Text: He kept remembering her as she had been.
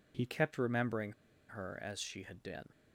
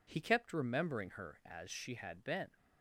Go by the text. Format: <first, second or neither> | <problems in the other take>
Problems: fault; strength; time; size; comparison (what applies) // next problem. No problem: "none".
second | pauses between "remembering" and "her"; at 1.1 s; 0.37 s long